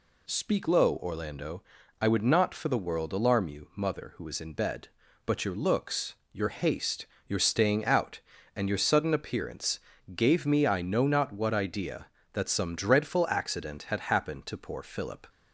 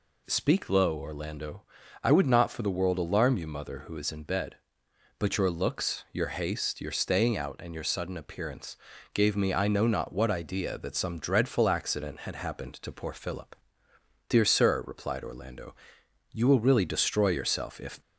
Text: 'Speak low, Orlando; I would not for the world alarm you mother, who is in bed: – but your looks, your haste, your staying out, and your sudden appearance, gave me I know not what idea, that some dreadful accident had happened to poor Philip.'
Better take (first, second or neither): first